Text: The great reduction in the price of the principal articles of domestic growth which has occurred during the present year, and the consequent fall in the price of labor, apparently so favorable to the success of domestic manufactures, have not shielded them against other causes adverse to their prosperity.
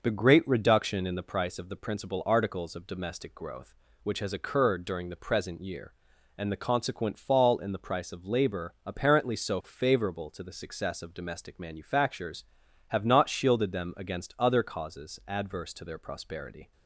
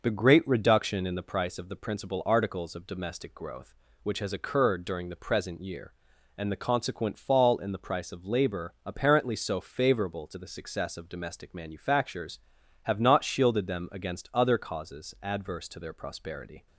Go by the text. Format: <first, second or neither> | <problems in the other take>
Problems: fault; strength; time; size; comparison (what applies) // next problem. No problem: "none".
neither | none